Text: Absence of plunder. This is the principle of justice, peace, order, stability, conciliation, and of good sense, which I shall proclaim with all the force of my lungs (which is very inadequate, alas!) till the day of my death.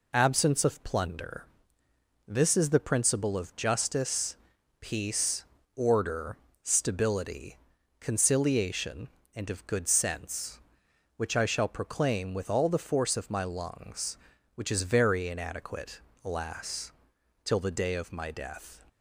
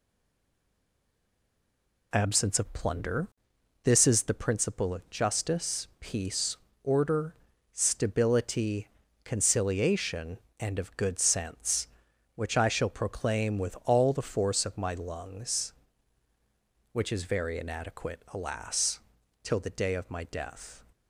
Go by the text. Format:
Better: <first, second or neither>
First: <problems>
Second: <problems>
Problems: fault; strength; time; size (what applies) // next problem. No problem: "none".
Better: first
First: none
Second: stays silent before the first word; until 2.1 s; 2.1 s long